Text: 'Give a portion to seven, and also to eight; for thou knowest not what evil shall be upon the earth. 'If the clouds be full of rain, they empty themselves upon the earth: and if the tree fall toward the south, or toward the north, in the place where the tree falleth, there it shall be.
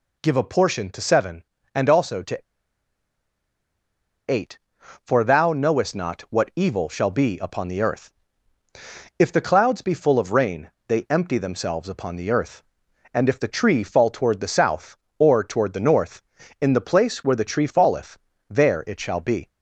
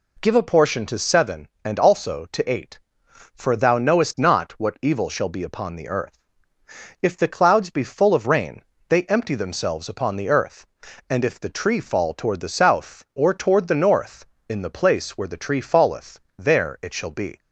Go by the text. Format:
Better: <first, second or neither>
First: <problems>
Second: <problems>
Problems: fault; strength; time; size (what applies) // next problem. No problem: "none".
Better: second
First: pauses between "to" and "eight"; strong; at 2.3 s; 1.8 s long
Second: none